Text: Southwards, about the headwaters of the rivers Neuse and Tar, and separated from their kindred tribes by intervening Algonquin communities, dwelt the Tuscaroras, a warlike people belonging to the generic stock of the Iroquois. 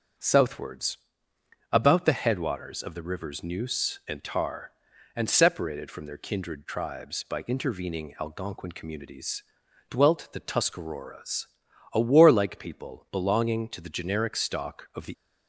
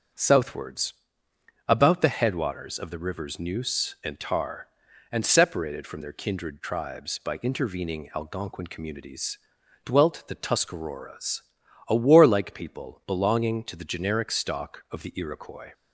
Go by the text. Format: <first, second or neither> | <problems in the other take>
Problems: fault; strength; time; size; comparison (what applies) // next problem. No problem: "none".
second | starts louder than the rest; strong; until 1.9 s; 7 dB; also in the second // stops before "Iroquois"; at 15.1 s